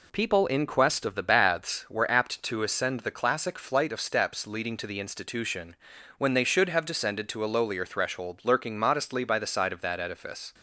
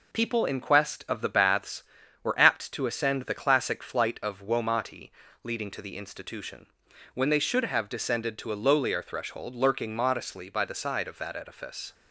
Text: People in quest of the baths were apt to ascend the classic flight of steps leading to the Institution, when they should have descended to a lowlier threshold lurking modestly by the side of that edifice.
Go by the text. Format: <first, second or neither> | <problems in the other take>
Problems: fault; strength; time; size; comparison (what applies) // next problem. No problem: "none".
first | says "womati" for "steps"; at 4.4 s